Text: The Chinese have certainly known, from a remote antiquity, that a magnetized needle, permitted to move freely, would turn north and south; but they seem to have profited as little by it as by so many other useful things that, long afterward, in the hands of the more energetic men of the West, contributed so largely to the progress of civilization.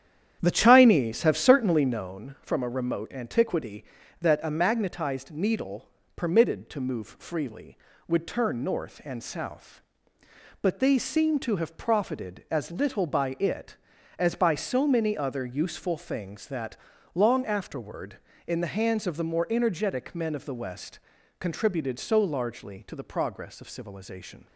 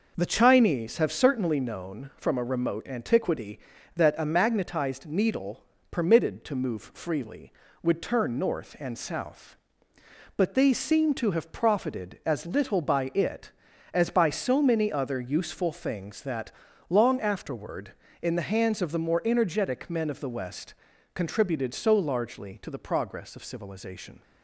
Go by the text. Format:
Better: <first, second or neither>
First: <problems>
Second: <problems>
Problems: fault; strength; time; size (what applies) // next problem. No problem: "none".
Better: second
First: starts louder than the rest; strong; until 2.1 s; 9.5 dB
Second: none